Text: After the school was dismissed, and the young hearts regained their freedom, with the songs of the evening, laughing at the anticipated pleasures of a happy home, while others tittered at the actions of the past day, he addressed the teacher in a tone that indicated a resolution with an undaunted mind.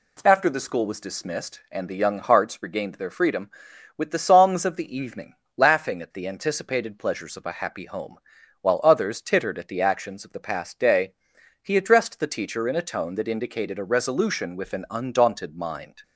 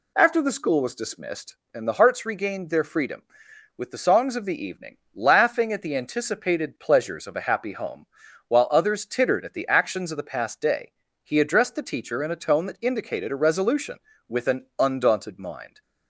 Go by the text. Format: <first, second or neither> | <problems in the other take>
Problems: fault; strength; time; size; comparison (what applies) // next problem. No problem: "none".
first | skips "young"; at 1.9 s